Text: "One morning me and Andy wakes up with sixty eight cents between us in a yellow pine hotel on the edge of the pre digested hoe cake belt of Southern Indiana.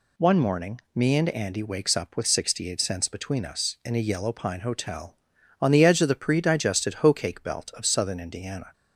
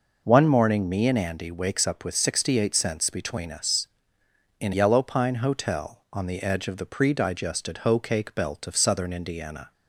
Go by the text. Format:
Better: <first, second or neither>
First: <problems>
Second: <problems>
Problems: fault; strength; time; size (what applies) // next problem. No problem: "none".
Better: first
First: none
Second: skips "a"; at 4.7 s